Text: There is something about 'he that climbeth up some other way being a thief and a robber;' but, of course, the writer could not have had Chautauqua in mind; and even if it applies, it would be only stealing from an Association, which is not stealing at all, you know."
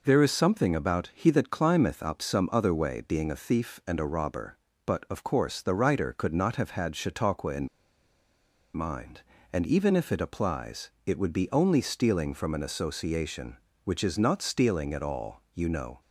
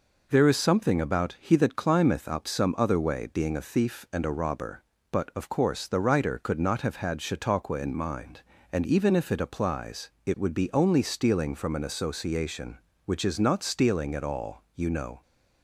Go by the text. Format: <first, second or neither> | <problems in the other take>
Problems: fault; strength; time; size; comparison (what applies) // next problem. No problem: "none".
second | pauses between "in" and "mind"; at 7.6 s; 1.0 s long